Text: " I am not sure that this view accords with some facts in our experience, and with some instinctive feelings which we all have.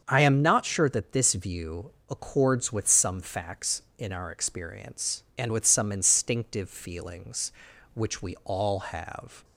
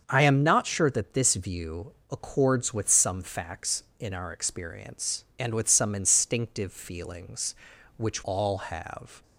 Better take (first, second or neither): first